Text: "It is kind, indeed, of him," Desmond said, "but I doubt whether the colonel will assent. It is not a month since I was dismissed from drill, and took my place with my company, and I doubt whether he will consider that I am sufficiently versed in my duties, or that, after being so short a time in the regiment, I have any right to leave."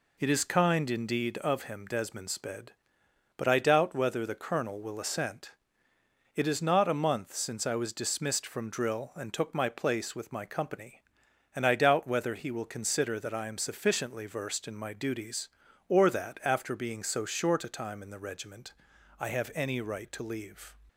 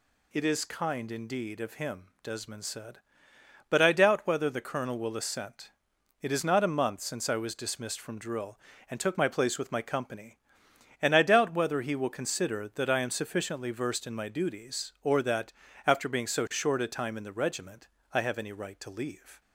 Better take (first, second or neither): second